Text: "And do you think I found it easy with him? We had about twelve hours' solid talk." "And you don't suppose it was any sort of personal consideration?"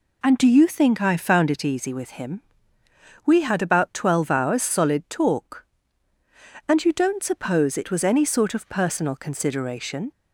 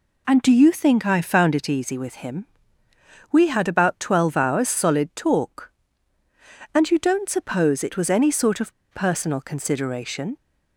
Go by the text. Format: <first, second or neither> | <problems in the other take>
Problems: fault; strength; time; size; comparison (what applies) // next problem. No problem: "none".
first | pauses between "of" and "personal"; slight; at 8.7 s; 0.22 s long